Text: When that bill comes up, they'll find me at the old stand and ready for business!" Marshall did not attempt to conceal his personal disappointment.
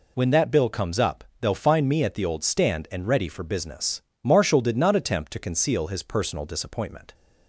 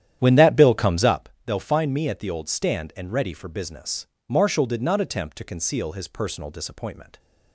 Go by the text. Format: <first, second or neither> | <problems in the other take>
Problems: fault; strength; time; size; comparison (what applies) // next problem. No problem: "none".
first | starts louder than the rest; strong; until 1.3 s; 10.5 dB